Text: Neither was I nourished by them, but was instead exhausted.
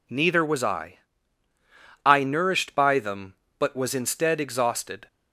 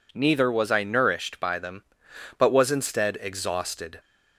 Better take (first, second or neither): second